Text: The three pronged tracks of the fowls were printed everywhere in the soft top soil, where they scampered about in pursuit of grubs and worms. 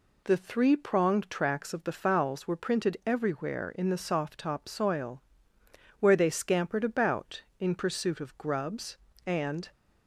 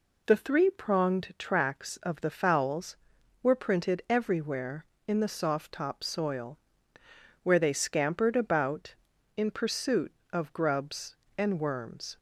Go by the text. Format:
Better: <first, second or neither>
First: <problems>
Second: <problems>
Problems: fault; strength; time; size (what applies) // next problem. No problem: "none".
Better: second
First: stops before "worms"; at 9.7 s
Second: none